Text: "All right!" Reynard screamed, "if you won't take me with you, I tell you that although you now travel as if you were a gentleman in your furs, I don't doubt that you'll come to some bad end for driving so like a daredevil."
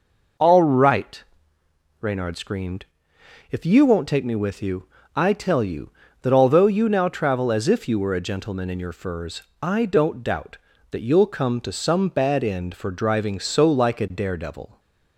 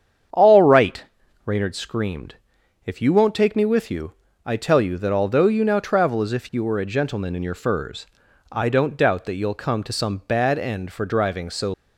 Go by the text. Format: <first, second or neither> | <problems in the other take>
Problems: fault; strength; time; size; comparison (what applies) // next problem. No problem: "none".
first | starts louder than the rest; strong; until 1.7 s; 8 dB // stops before "like a daredevil"; at 11.7 s